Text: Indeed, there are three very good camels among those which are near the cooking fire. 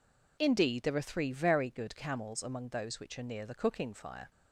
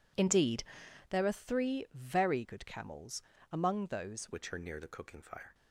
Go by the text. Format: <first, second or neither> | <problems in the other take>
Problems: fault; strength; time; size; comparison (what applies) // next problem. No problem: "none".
first | pauses between "camels" and "among"; slight; at 3.2 s; 0.30 s long // changes voice at "which"; from 4.3 s on; 1.2 s long